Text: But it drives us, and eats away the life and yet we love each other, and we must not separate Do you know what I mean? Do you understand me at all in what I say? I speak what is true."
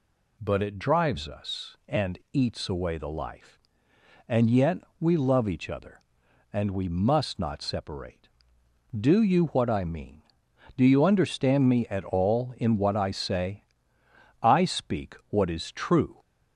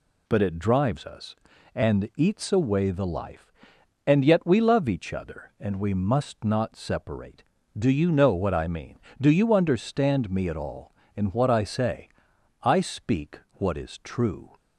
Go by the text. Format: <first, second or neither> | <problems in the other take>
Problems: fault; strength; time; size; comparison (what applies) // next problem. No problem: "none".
second | pauses between "yet" and "we"; slight; at 4.7 s; 0.24 s long // skips "know"; at 9.4 s